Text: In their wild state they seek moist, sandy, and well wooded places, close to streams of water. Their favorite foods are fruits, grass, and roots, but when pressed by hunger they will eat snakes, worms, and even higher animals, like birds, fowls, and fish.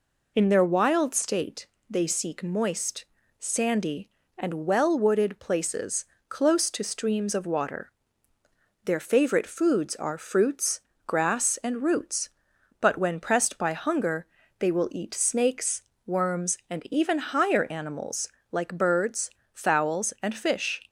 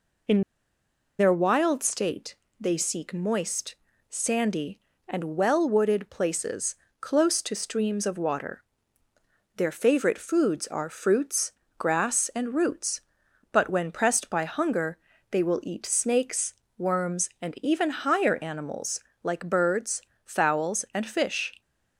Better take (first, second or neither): first